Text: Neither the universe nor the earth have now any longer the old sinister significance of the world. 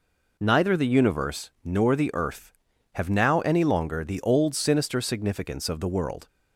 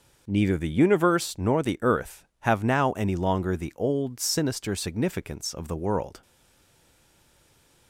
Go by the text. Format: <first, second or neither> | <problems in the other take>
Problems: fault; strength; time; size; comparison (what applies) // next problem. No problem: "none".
first | starts louder than the rest; noticeable; until 1.2 s; 6 dB // stays silent after the last word; noticeable; from 6.2 s on; 1.6 s long